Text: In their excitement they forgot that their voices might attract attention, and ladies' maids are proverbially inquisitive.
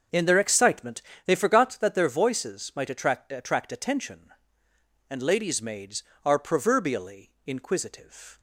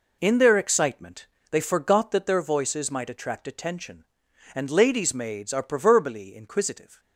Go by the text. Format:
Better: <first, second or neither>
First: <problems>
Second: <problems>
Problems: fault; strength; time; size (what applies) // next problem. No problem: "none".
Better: second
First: starts louder than the rest; until 1.3 s; 6.5 dB // pauses between "excitement" and "they"; slight; at 1.0 s; 0.24 s long // says "attract" twice; at 3.3 s // pauses between "proverbially" and "inquisitive"; slight; at 7.2 s; 0.16 s long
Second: pauses between "excitement" and "they"; slight; at 1.2 s; 0.22 s long